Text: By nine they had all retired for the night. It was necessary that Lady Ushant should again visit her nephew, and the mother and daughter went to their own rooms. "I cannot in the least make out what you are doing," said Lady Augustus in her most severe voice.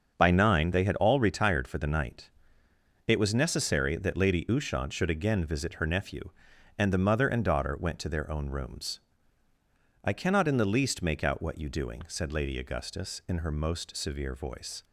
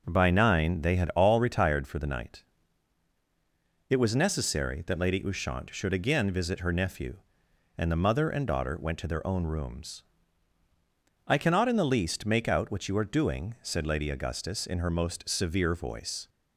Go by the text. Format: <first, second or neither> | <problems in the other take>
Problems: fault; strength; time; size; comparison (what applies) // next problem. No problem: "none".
second | starts louder than the rest; until 1.1 s; 6.5 dB // skips "are"; at 11.6 s